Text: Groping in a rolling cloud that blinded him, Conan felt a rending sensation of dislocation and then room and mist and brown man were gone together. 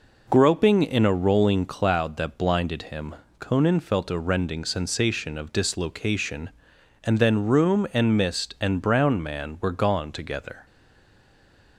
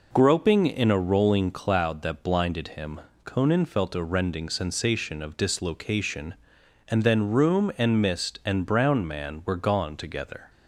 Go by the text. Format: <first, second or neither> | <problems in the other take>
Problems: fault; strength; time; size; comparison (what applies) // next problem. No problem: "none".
second | stays silent after the last word; from 10.6 s on; 1.1 s long